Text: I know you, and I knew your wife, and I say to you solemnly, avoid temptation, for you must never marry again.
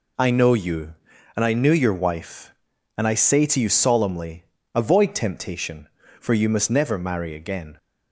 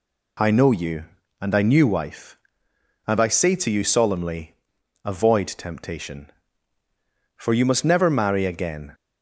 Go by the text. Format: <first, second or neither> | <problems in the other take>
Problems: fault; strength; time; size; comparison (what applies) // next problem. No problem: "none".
first | skips "your"; at 1.8 s